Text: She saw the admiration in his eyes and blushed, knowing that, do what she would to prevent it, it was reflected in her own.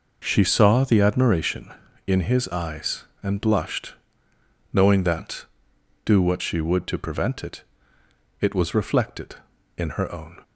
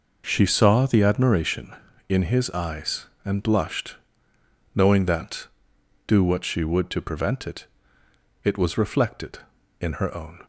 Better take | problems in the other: neither | none

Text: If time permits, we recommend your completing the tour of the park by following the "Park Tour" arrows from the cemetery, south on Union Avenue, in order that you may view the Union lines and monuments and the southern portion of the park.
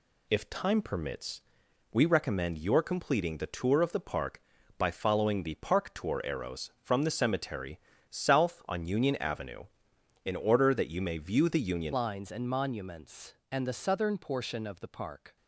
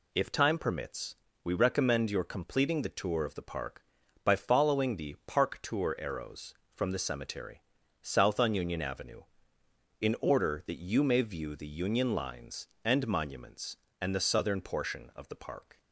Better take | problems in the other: second | changes voice at "lines"; from 11.9 s on; 3.4 s long

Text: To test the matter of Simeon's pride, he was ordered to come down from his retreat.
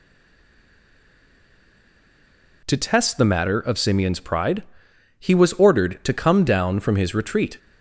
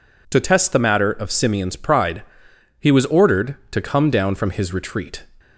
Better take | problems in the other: second | stays silent before the first word; strong; until 2.6 s; 2.6 s long

